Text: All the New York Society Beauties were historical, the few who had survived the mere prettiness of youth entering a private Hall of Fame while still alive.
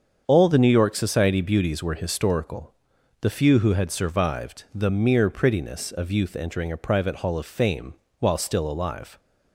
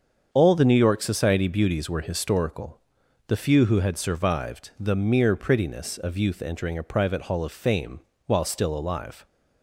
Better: neither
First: starts louder than the rest; strong; until 1.2 s; 7 dB // pauses between "Fame" and "while"; slight; at 7.9 s; 0.29 s long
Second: starts louder than the rest; strong; until 1.3 s; 7 dB // pauses between "Fame" and "while"; slight; at 7.9 s; 0.30 s long

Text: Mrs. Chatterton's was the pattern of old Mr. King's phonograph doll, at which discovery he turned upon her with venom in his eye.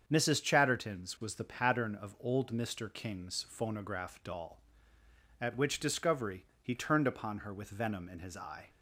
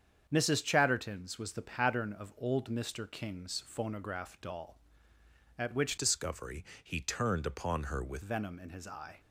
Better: first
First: starts louder than the rest; strong; until 1.0 s; 7 dB // pauses between "discovery" and "he"; slight; at 6.4 s; 0.18 s long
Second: starts louder than the rest; strong; until 1.3 s; 7.5 dB // changes voice from "discovery" to "with"; from 5.9 to 8.2 s; 2.3 s long // pauses between "discovery" and "he"; slight; at 6.6 s; 0.18 s long

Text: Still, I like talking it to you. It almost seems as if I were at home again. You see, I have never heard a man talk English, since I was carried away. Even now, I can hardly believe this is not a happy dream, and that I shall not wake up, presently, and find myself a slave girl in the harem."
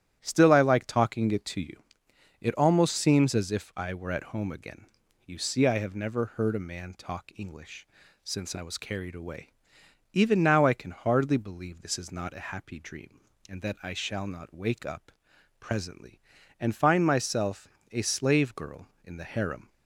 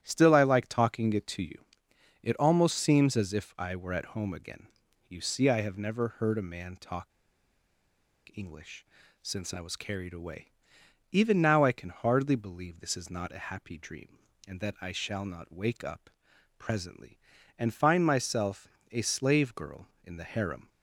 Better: first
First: starts louder than the rest; strong; until 1.2 s; 10.5 dB // pauses between "myself" and "a"; slight; at 17.6 s; 0.24 s long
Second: starts louder than the rest; strong; until 1.0 s; 10.5 dB // pauses between "talk" and "English"; at 7.1 s; 1.2 s long // pauses between "myself" and "a"; slight; at 18.6 s; 0.24 s long

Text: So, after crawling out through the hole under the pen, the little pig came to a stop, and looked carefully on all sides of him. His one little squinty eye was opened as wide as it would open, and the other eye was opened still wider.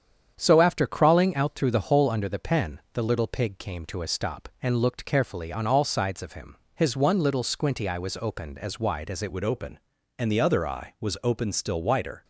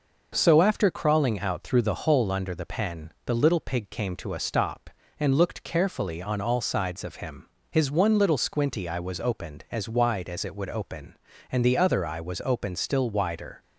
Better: second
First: starts louder than the rest; strong; until 1.4 s; 8.5 dB // changes voice at "would"; from 9.3 s on; 2.9 s long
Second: none

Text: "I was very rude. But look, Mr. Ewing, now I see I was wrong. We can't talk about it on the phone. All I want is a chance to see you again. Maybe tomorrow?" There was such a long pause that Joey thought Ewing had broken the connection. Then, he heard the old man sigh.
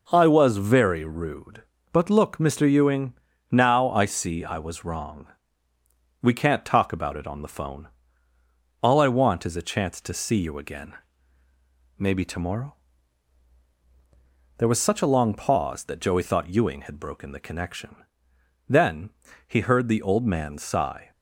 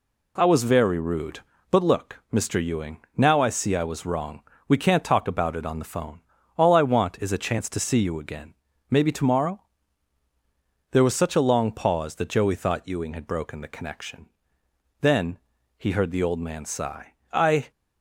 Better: first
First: none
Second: goes on to say "I"; slight; from 17.3 s on; 0.38 s long

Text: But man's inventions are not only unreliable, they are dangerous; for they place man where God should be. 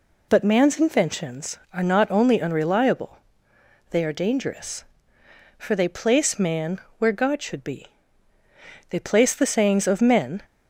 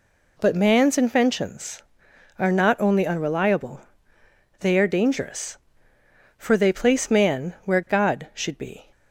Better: second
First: pauses between "man" and "where"; slight; at 6.7 s; 0.20 s long // goes on to say "They place the sayings of men"; from 8.9 s on; 1.5 s long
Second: none

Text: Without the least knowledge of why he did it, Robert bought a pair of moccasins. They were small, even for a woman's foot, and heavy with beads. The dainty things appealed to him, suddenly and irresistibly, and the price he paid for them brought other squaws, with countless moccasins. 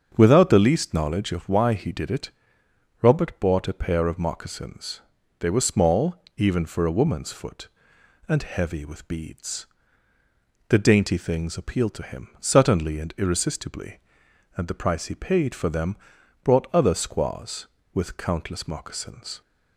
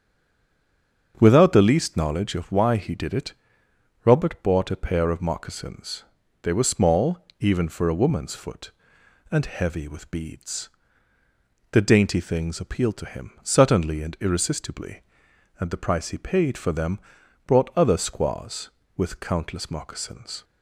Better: first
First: starts louder than the rest; until 1.1 s; 7 dB // pauses between "them" and "brought"; noticeable; at 15.9 s; 0.46 s long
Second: stays silent before the first word; until 1.1 s; 1.1 s long // starts louder than the rest; until 2.1 s; 7 dB // pauses between "them" and "brought"; noticeable; at 16.9 s; 0.46 s long

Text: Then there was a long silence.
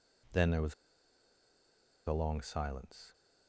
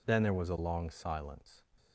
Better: second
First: pauses between "was" and "a"; strong; at 0.7 s; 1.3 s long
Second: none

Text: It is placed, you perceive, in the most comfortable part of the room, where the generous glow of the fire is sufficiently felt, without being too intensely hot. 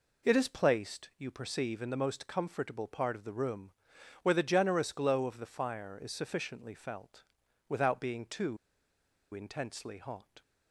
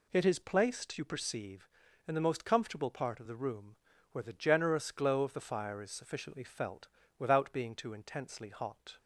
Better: second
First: pauses between "too" and "intensely"; noticeable; at 8.5 s; 0.76 s long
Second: none

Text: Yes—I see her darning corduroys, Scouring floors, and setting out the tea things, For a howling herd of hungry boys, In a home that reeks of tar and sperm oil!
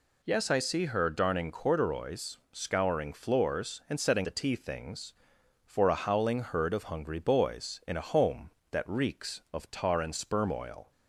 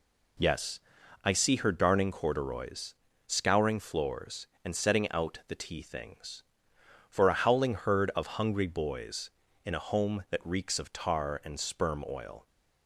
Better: second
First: skips "out"; at 4.2 s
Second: none

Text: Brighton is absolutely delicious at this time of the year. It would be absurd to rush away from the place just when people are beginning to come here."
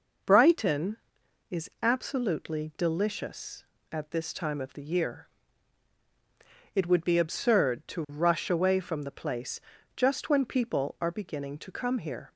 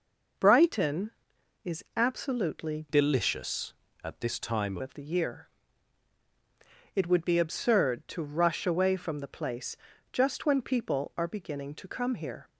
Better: first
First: pauses between "place" and "just"; slight; at 9.6 s; 0.34 s long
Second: changes voice from "delicious" to "time"; from 2.8 to 4.7 s; 1.9 s long // pauses between "place" and "just"; slight; at 9.7 s; 0.34 s long

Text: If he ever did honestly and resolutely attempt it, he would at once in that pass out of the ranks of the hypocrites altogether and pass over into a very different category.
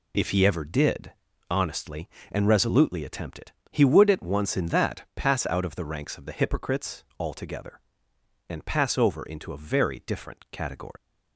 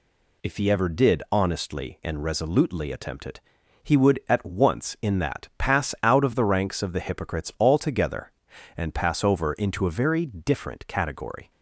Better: second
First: pauses between "did" and "honestly"; at 1.1 s; 0.38 s long // pauses between "hypocrites" and "altogether"; slight; at 7.0 s; 0.16 s long // leaves "category" unfinished; at 10.9 s; 125 ms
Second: none

